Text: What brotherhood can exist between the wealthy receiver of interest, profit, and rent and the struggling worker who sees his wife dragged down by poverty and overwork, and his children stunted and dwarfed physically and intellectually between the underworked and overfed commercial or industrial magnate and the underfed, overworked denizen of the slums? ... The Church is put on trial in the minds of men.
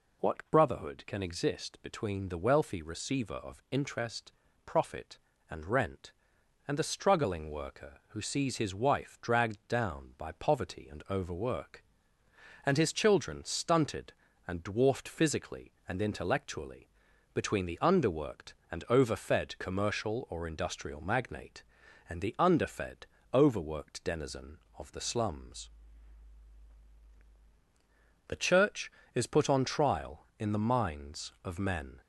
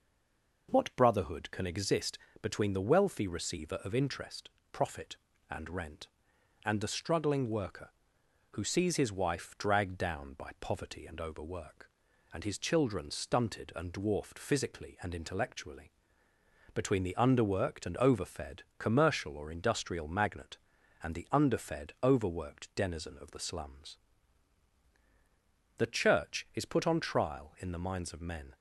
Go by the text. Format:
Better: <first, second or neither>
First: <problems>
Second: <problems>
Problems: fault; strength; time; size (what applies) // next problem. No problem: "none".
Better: first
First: pauses between "intellectually" and "between"; noticeable; at 16.8 s; 0.46 s long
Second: stays silent before the first word; slight; until 0.6 s; 0.6 s long // pauses between "exist" and "between"; slight; at 2.1 s; 0.24 s long // pauses between "intellectually" and "between"; noticeable; at 15.8 s; 0.86 s long // pauses between "overfed" and "commercial"; slight; at 18.6 s; 0.16 s long